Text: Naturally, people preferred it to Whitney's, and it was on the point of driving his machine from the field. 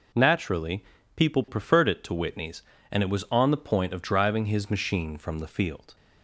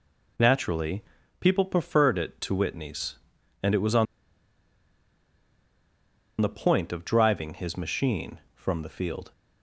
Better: first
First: none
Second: pauses between "on" and "the"; strong; at 4.0 s; 2.3 s long

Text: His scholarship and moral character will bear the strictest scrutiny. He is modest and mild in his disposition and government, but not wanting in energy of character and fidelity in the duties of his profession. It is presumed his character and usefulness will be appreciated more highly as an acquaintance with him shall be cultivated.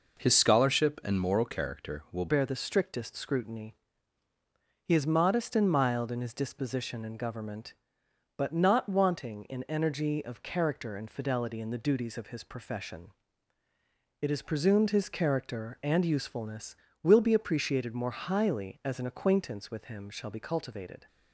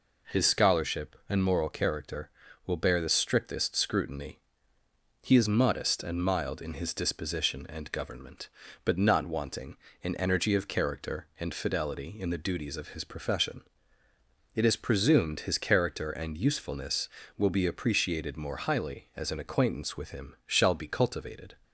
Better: second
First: changes voice at "bear"; from 2.2 s on; 18.8 s long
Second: none

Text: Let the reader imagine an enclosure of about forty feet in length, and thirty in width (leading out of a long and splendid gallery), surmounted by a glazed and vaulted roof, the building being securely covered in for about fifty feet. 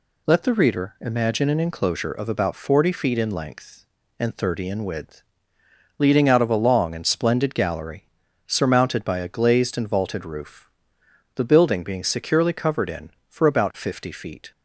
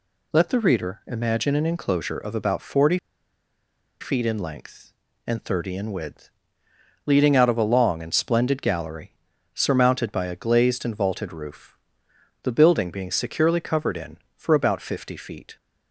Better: first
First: none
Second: pauses between "forty" and "feet"; at 2.9 s; 1.0 s long

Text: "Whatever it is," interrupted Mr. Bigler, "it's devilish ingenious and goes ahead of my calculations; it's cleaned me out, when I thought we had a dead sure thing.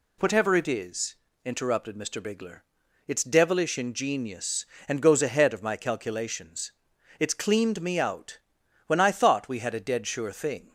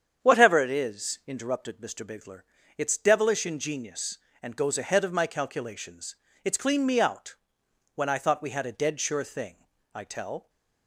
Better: first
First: none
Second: starts louder than the rest; strong; until 1.2 s; 8 dB // goes on to say "I tell"; from 9.9 s on; 0.54 s long

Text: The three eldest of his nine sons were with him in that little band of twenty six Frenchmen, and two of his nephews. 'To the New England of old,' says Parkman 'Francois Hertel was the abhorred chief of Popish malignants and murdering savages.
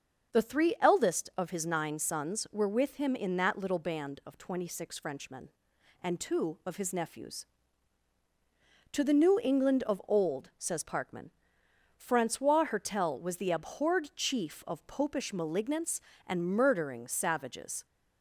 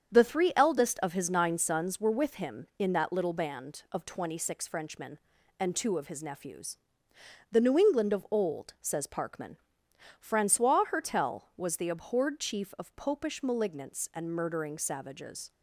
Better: first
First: starts louder than the rest; until 1.4 s; 7 dB // pauses between "Parkman" and "Francois"; noticeable; at 11.3 s; 0.64 s long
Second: starts louder than the rest; strong; until 1.2 s; 7.5 dB // skips "To"; at 7.1 s // pauses between "Parkman" and "Francois"; noticeable; at 9.5 s; 0.62 s long

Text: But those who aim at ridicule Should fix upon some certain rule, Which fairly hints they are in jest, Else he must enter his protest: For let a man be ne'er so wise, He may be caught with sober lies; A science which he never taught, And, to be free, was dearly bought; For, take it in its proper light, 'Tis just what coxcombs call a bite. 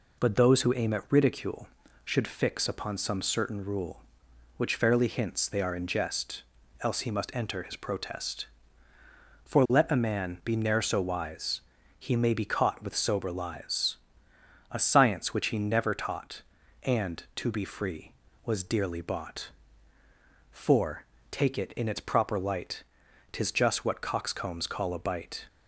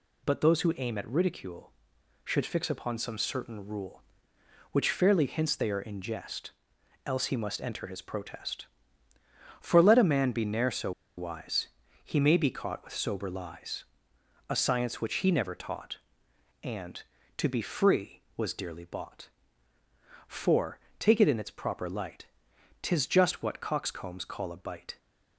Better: first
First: none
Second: pauses between "so" and "wise"; slight; at 10.9 s; 0.26 s long

